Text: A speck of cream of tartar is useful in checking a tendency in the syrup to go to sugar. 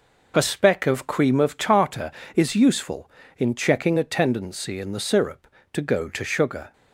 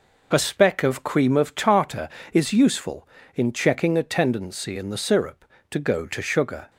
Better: neither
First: none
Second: none

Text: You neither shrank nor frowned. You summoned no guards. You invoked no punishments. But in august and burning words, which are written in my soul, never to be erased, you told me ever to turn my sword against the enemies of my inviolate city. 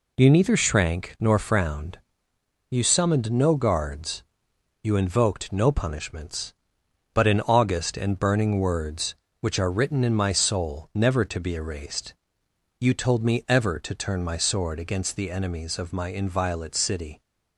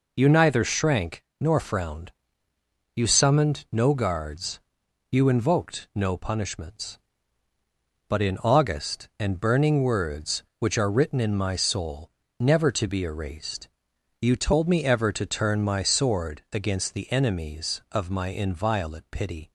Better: first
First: none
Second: pauses between "shrank" and "nor"; slight; at 1.2 s; 0.16 s long // says "pity" for "city"; at 19.1 s

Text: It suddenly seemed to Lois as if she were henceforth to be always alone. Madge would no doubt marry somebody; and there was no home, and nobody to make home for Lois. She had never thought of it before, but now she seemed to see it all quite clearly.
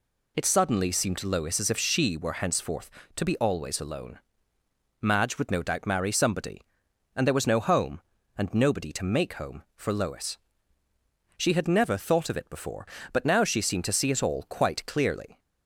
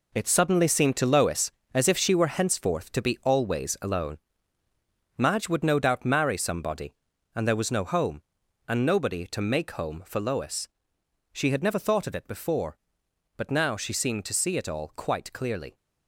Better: first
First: none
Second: gets quieter; strong; throughout; 9 dB

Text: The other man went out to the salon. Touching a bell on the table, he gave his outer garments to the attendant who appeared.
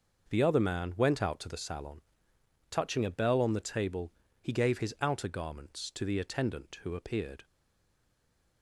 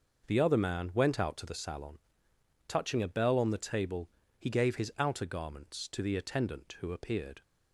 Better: second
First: starts louder than the rest; noticeable; until 1.3 s; 6 dB // stays silent after the last word; noticeable; from 7.4 s on; 1.2 s long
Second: starts louder than the rest; noticeable; until 1.3 s; 6 dB

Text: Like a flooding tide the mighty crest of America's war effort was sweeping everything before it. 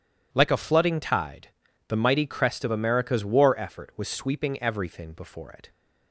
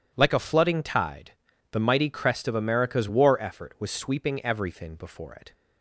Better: neither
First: pauses between "tide" and "the"; at 1.4 s; 0.40 s long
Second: pauses between "tide" and "the"; at 1.3 s; 0.40 s long

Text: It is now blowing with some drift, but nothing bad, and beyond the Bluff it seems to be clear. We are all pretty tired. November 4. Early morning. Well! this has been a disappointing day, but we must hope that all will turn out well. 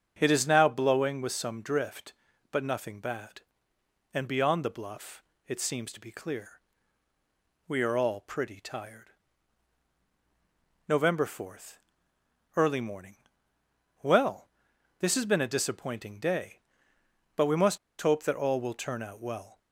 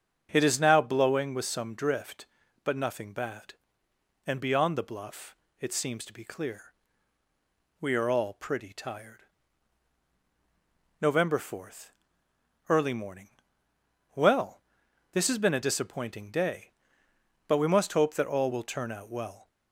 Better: second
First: starts louder than the rest; strong; until 1.2 s; 7.5 dB // pauses between "Bluff" and "it"; slight; at 5.2 s; 0.26 s long // pauses between "must" and "hope"; slight; at 17.7 s; 0.23 s long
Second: starts louder than the rest; strong; until 1.3 s; 7.5 dB // pauses between "Bluff" and "it"; slight; at 5.3 s; 0.26 s long

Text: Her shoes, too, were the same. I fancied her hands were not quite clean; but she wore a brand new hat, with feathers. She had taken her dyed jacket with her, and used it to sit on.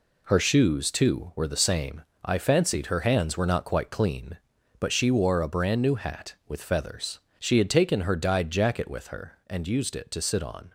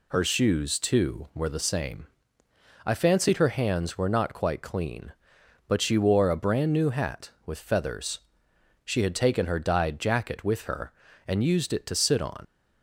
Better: first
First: none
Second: leaves "on" unfinished; at 12.4 s; 75 ms

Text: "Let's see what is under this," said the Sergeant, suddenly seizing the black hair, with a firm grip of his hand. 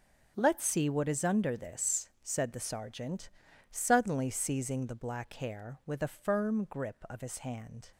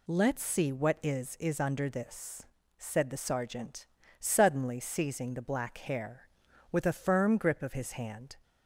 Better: first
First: none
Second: says "is" twice; at 1.3 s

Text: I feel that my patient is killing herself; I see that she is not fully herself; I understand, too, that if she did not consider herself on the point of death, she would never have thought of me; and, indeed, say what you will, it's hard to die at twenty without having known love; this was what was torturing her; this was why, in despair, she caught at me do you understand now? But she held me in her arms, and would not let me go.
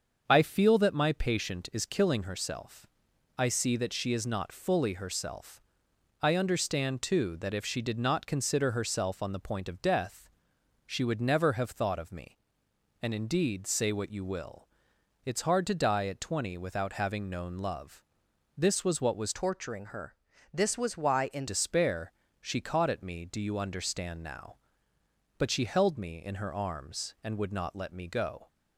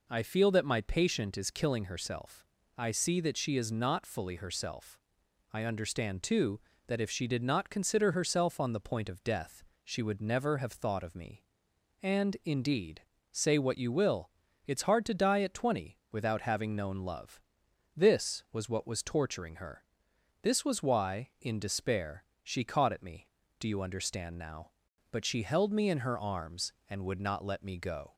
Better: second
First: starts louder than the rest; until 1.2 s; 6.5 dB // changes voice from "torturing" to "in"; from 19.3 to 21.4 s; 2.1 s long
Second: none

